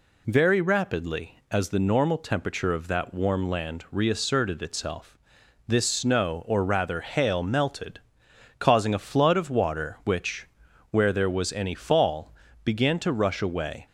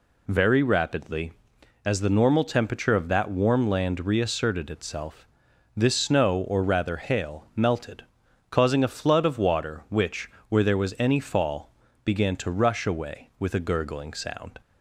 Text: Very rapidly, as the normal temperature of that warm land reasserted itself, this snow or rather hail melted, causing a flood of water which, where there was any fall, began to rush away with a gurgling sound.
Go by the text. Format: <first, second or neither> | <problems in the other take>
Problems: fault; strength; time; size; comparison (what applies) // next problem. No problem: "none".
second | stops before "with a gurgling sound"; at 13.8 s